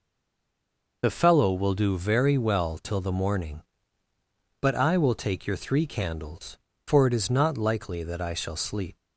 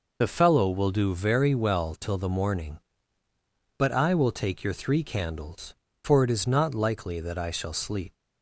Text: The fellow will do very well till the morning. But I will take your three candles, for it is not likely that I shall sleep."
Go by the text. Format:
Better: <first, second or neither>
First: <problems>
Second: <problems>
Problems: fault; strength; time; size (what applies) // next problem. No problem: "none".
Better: second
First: stays silent before the first word; until 1.0 s; 1.0 s long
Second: none